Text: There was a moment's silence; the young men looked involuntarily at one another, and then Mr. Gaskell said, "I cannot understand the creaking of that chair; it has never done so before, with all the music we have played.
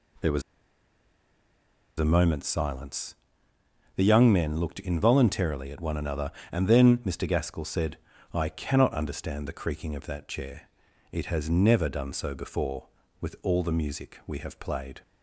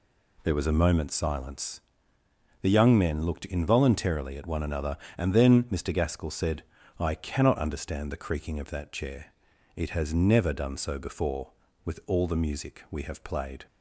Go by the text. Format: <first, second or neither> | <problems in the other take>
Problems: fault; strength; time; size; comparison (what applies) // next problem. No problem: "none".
second | pauses between "was" and "a"; strong; at 0.4 s; 1.5 s long